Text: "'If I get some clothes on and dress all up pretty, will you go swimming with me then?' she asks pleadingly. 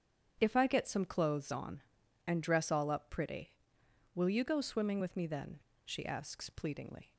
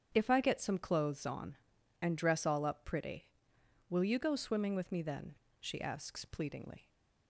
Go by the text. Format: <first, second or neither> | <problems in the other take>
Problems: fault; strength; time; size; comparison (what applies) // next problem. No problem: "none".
neither | starts louder than the rest; strong; the same in both